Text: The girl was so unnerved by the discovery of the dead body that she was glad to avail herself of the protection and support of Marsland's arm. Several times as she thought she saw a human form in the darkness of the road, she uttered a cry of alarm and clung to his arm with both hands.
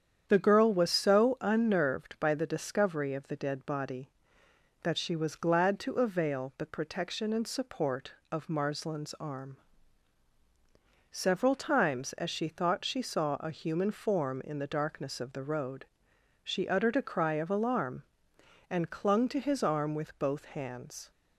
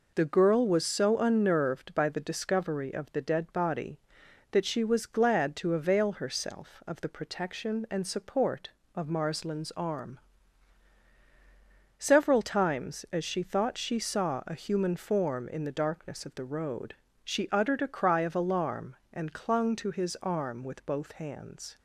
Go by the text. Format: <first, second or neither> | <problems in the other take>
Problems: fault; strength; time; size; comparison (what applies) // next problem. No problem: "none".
second | starts louder than the rest; strong; until 1.2 s; 8.5 dB // skips "herself of"; at 6.5 s